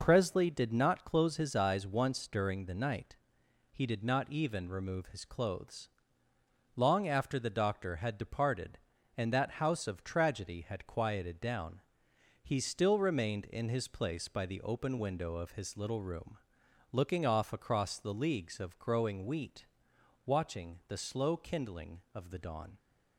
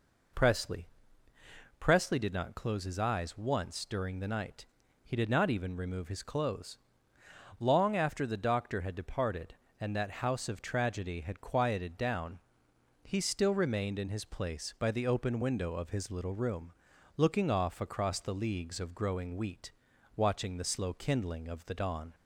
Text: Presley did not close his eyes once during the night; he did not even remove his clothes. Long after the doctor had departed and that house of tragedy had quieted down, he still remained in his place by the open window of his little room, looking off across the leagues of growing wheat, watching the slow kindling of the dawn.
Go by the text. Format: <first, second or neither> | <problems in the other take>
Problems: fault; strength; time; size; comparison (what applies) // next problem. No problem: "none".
first | says "Presley" twice; at 1.8 s